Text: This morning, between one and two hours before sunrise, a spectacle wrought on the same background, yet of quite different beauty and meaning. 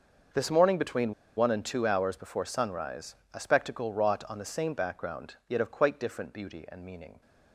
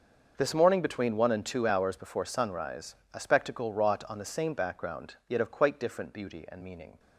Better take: second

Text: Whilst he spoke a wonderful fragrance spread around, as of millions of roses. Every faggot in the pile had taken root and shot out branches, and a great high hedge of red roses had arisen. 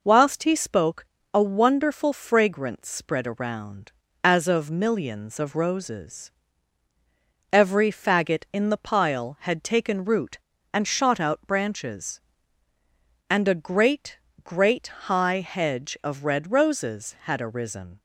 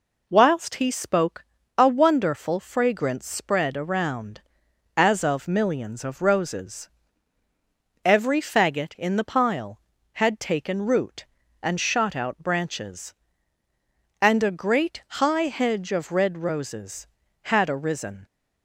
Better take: second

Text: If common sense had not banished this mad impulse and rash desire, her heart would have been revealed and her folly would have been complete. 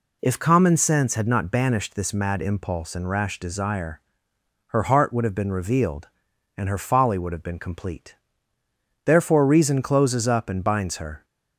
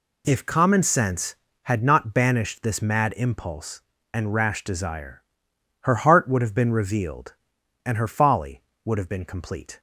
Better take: second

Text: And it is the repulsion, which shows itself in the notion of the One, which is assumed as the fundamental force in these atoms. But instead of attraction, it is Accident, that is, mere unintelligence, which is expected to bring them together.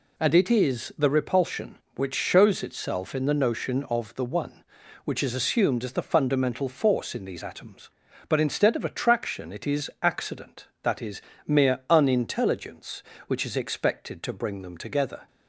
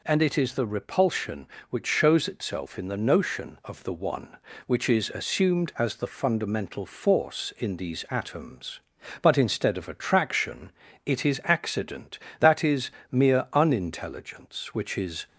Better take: first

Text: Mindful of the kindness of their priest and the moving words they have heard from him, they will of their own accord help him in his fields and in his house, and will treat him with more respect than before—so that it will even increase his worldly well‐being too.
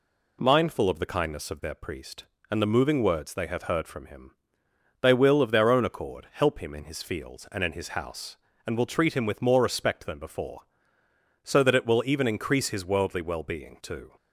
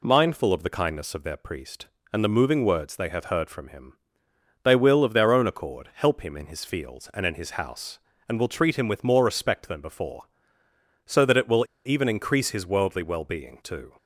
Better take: first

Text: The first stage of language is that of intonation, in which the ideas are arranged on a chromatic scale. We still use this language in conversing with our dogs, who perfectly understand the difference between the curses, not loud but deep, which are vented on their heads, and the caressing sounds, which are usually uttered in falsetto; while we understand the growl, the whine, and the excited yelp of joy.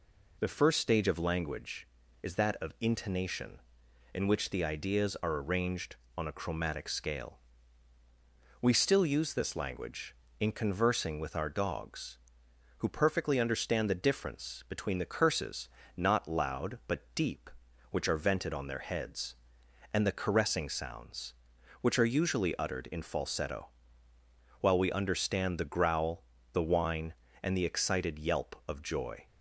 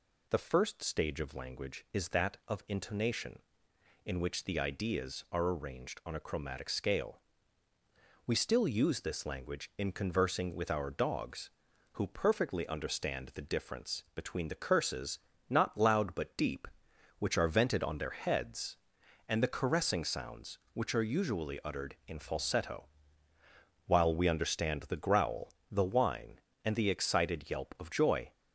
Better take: neither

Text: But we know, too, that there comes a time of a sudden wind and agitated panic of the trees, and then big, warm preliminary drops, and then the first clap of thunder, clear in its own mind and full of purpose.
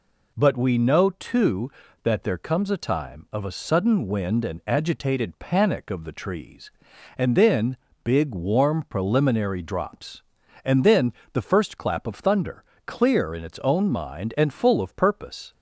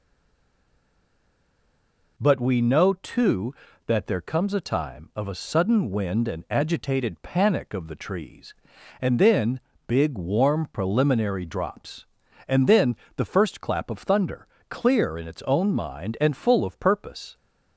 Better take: first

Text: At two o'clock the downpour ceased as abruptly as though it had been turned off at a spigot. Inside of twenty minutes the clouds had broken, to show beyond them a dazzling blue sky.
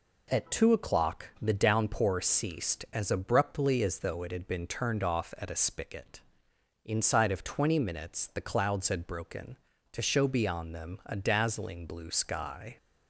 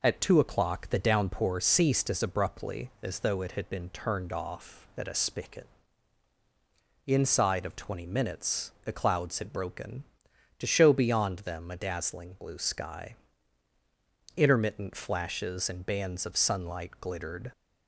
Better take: first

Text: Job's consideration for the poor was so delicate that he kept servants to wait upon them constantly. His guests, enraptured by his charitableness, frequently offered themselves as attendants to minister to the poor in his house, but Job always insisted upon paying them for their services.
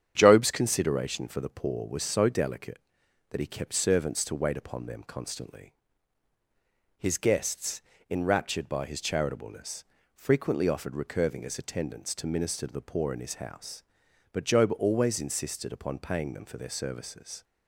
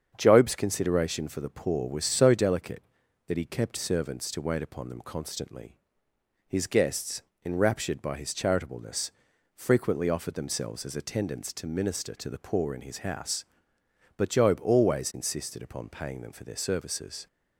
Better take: second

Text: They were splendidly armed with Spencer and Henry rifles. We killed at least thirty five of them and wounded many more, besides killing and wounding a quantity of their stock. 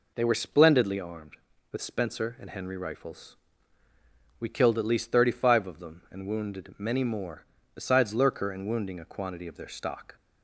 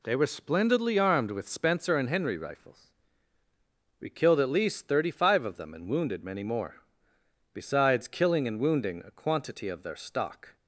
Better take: second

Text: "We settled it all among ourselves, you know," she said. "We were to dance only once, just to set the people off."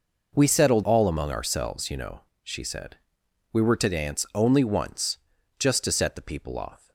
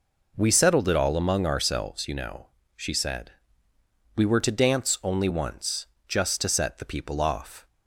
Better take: second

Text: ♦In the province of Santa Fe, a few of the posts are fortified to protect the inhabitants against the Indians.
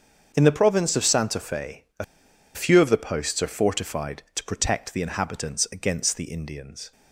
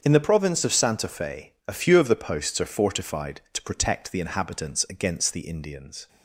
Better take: second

